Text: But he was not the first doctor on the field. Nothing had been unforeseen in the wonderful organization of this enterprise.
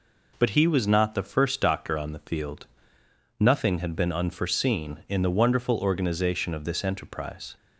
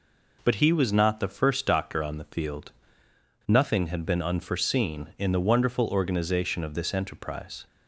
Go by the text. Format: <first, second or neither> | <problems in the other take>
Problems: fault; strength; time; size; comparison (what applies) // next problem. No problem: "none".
neither | none